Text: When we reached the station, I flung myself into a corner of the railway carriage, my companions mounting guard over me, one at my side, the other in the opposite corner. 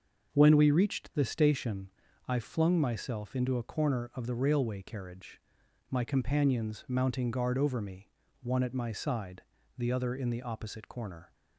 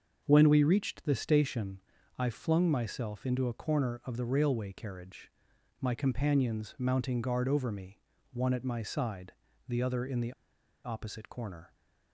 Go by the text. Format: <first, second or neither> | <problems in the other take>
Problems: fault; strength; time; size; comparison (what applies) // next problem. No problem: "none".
first | starts louder than the rest; until 1.2 s; 6.5 dB; also in the first // pauses between "the" and "opposite"; noticeable; at 10.3 s; 0.53 s long